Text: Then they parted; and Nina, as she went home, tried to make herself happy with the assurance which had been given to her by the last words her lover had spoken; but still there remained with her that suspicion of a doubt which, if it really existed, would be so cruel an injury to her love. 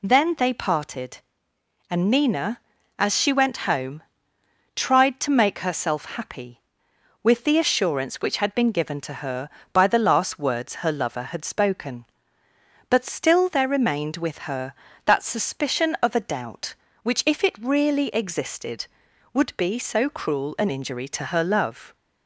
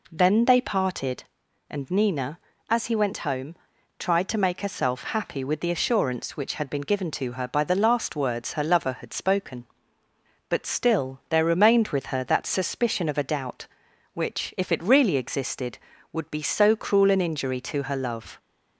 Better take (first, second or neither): first